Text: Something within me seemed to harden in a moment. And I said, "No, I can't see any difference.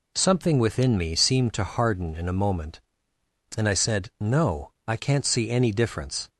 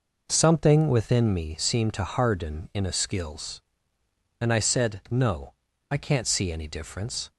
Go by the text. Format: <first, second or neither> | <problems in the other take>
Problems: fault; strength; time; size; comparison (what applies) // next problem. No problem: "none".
first | says "skills" for "moment"; at 2.9 s